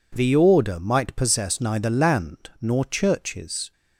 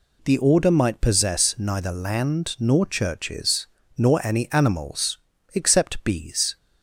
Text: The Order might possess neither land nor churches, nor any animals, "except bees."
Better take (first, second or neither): second